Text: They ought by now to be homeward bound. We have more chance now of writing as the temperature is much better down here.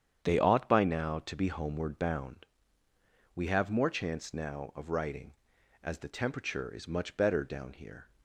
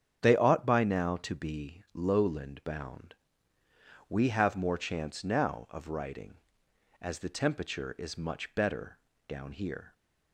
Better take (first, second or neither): first